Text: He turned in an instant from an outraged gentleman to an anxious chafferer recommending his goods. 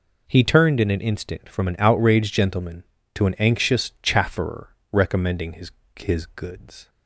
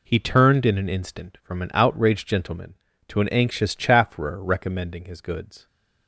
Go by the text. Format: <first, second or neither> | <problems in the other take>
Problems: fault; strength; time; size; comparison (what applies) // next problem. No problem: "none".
second | pauses between "chafferer" and "recommending"; slight; at 4.6 s; 0.24 s long // says "his" twice; at 5.9 s